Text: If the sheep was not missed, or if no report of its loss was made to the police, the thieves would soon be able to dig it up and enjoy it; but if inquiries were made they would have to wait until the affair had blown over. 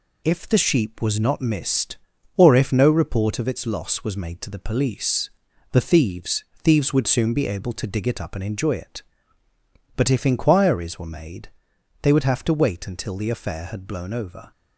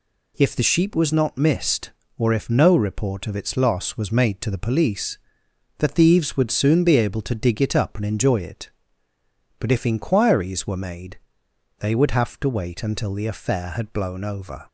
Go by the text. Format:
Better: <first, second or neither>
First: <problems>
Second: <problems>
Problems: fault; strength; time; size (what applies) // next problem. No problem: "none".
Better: second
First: says "thieves" twice; at 6.6 s // pauses between "made" and "they"; noticeable; at 11.4 s; 0.54 s long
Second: pauses between "made" and "they"; noticeable; at 11.1 s; 0.60 s long